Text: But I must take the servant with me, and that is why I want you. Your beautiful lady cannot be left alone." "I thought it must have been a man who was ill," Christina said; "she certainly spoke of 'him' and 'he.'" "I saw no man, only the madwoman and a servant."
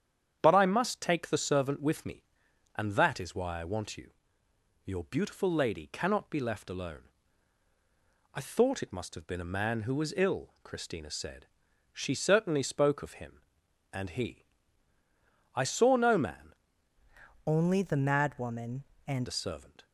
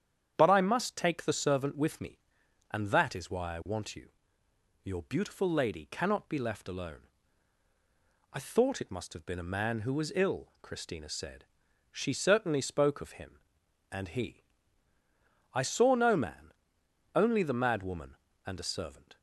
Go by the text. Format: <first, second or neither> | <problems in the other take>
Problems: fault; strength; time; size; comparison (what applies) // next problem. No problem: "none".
second | starts louder than the rest; strong; until 1.4 s; 9 dB; strong in the second // changes voice from "only" to "and"; from 17.4 to 19.2 s; 1.8 s long